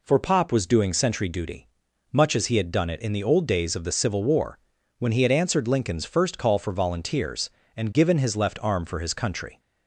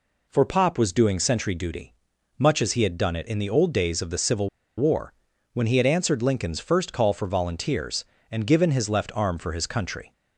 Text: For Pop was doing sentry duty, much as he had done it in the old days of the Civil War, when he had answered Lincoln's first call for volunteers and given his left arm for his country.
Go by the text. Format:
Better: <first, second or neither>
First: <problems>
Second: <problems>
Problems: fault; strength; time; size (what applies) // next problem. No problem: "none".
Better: first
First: none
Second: pauses between "Civil" and "War"; slight; at 4.4 s; 0.29 s long